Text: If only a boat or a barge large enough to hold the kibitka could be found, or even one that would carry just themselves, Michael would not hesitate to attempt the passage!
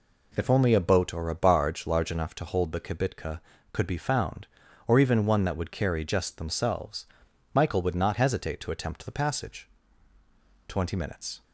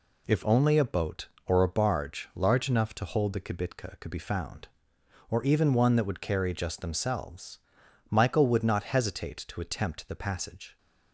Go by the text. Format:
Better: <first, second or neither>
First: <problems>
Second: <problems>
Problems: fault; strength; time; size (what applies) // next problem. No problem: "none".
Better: second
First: goes on to say "Twenty minutes"; noticeable; from 10.6 s on; 0.76 s long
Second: none